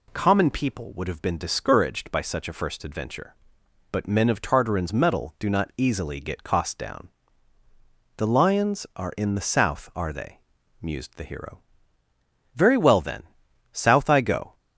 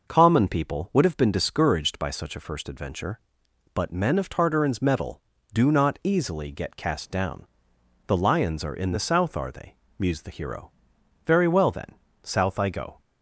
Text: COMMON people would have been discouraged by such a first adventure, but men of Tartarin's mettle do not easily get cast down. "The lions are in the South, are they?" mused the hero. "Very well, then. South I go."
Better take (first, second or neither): second